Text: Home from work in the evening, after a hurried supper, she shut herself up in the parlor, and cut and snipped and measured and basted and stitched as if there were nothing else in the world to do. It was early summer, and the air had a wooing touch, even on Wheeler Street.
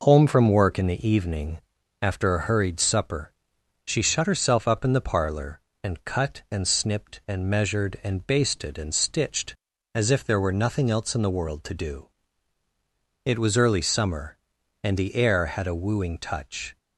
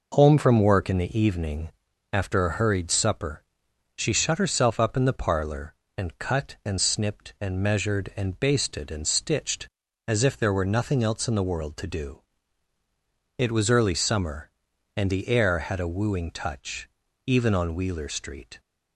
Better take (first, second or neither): second